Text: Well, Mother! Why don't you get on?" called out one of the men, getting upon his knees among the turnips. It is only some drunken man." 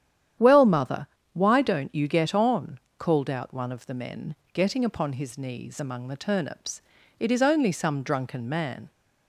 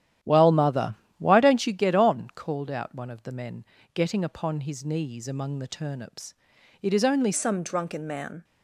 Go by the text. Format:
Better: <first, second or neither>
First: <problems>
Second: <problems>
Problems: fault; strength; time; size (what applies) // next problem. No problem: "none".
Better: first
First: starts louder than the rest; strong; until 1.6 s; 10 dB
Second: starts louder than the rest; strong; until 1.4 s; 11 dB // changes voice at "some"; from 7.3 s on; 1.1 s long